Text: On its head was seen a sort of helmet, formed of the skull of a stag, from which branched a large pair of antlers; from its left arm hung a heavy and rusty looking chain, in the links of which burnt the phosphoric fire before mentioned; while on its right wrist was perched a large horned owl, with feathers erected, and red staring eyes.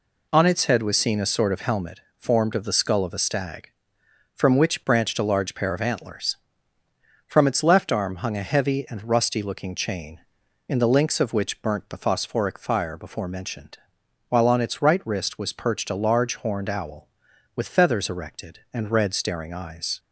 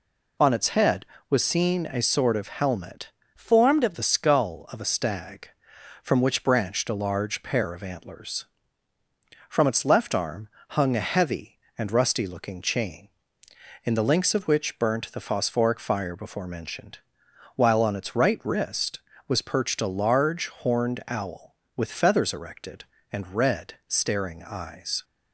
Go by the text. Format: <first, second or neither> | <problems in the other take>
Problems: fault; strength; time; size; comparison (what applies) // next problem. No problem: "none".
first | changes voice from "formed" to "of"; from 3.3 to 3.9 s; 0.6 s long // pauses between "arm" and "hung"; slight; at 10.4 s; 0.22 s long